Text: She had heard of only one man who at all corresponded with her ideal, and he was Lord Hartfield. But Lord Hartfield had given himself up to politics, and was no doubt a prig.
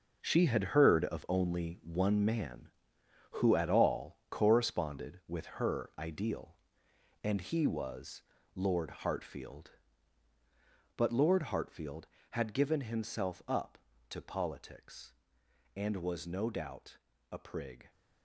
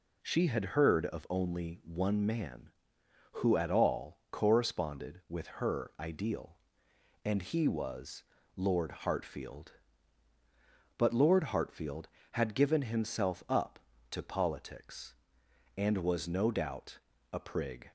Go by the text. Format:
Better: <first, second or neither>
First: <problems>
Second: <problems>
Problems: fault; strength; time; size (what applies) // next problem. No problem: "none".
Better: second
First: gets quieter; strong; throughout; 9.5 dB // pauses between "was" and "Lord"; slight; at 8.2 s; 0.32 s long // pauses between "doubt" and "a"; slight; at 16.9 s; 0.34 s long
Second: pauses between "was" and "Lord"; slight; at 8.2 s; 0.32 s long // pauses between "doubt" and "a"; slight; at 16.9 s; 0.34 s long